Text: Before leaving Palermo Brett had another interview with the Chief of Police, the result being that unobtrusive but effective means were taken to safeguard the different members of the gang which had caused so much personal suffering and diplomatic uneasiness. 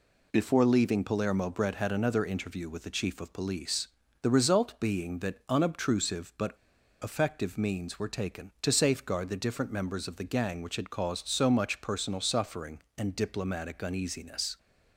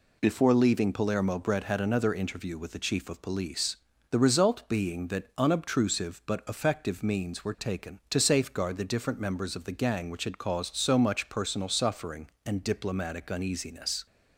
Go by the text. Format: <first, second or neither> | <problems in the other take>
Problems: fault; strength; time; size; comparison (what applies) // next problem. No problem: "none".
second | pauses between "but" and "effective"; noticeable; at 6.5 s; 0.47 s long